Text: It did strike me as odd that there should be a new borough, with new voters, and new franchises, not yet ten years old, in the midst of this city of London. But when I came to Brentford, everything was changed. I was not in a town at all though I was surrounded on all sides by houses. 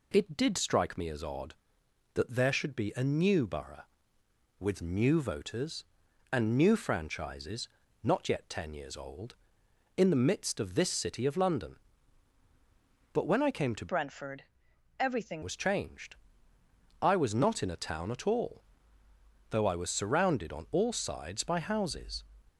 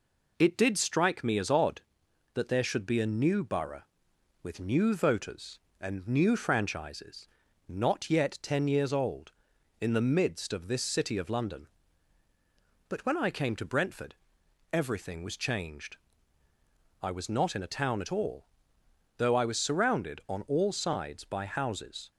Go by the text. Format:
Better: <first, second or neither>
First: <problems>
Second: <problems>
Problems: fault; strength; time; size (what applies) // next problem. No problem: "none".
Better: second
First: changes voice from "Brentford" to "everything"; from 13.8 to 15.4 s; 1.6 s long // pauses between "all" and "though"; noticeable; at 18.6 s; 0.88 s long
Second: pauses between "all" and "though"; noticeable; at 18.4 s; 0.72 s long